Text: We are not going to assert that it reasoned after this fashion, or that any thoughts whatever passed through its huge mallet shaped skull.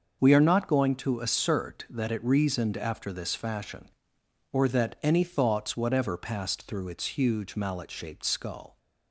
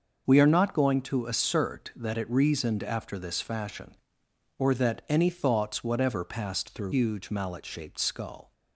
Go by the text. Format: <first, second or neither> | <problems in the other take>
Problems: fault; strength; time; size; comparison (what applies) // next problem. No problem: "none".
first | starts louder than the rest; until 1.3 s; 6 dB; also in the first // skips "its"; at 6.9 s